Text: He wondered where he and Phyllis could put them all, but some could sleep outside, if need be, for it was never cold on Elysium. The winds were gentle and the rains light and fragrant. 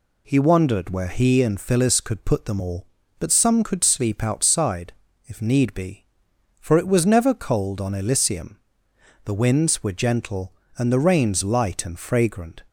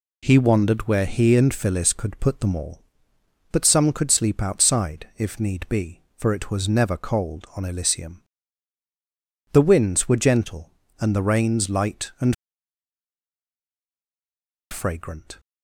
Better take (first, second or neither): first